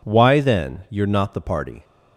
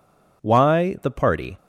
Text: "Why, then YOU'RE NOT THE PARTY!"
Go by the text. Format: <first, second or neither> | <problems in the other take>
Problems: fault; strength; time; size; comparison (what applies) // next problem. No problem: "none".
first | skips "then YOU'RE NOT"; at 0.9 s